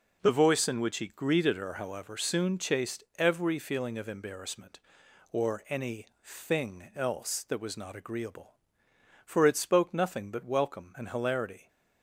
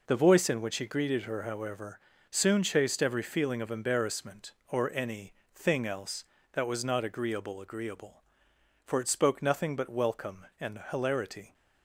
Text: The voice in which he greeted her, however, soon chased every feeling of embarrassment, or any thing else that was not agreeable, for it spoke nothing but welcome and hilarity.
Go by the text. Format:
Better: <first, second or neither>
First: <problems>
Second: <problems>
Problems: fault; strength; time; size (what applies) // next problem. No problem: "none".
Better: first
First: none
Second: pauses between "any" and "thing"; slight; at 5.3 s; 0.22 s long // says "agreeable" twice; at 7.5 s